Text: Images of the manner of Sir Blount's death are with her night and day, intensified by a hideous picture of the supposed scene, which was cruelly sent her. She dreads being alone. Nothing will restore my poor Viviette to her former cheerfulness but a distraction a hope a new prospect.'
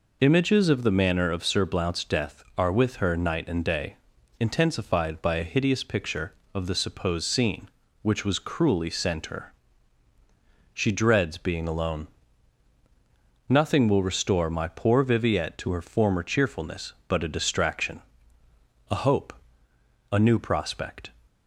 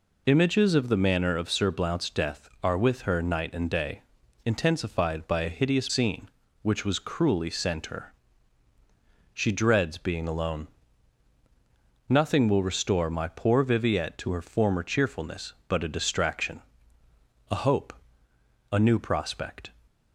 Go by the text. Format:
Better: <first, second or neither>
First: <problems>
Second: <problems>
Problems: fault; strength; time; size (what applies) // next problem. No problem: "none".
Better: first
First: pauses between "distraction" and "a"; noticeable; at 18.0 s; 0.88 s long // pauses between "hope" and "a"; noticeable; at 19.3 s; 0.80 s long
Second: skips "picture of the supposed"; at 5.8 s // pauses between "distraction" and "a"; noticeable; at 16.6 s; 0.88 s long // pauses between "hope" and "a"; noticeable; at 17.9 s; 0.80 s long